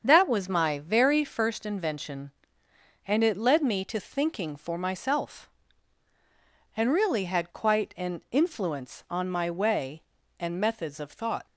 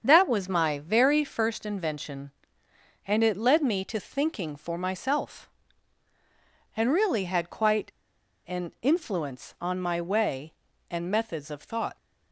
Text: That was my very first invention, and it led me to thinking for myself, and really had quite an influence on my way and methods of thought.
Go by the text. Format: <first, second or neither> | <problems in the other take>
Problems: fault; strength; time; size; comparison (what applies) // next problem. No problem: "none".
first | starts louder than the rest; until 1.0 s; 7 dB; also in the first // pauses between "quite" and "an"; noticeable; at 7.8 s; 0.59 s long